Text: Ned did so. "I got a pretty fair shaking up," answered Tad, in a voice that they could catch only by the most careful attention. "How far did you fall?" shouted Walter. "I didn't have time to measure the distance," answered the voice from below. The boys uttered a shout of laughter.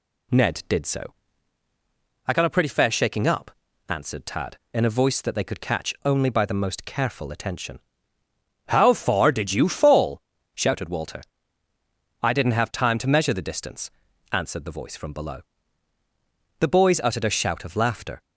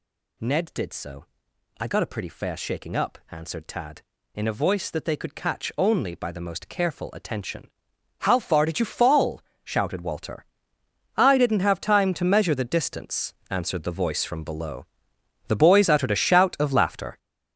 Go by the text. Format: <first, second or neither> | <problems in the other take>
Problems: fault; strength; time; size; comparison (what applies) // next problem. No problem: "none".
first | gets louder; strong; throughout; 9.5 dB